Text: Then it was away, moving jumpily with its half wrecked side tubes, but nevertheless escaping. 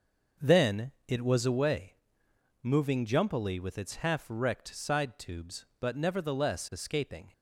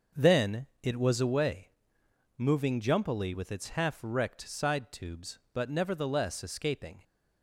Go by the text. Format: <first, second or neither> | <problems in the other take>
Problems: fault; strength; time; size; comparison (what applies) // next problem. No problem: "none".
neither | starts louder than the rest; noticeable; the same in both // pauses between "Then" and "it"; slight; the same in both